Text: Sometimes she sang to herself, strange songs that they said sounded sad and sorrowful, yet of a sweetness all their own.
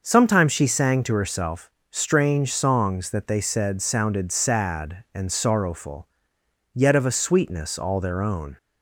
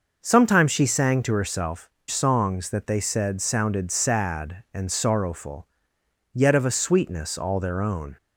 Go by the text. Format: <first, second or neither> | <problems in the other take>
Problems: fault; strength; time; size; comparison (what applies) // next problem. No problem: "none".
first | skips "strange"; at 2.0 s